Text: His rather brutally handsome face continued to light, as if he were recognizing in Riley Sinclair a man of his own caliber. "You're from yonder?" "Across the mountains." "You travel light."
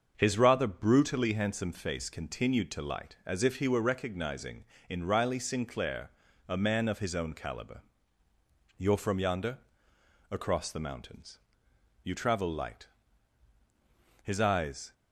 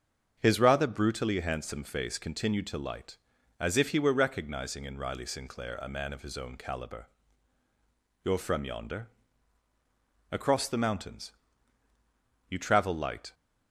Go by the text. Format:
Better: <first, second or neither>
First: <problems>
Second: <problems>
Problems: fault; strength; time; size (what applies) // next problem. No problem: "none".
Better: second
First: starts louder than the rest; until 1.1 s; 6.5 dB // pauses between "Sinclair" and "a"; at 6.0 s; 0.38 s long // goes on to say "His eyes"; noticeable; from 14.2 s on; 0.70 s long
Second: starts louder than the rest; strong; until 1.3 s; 7 dB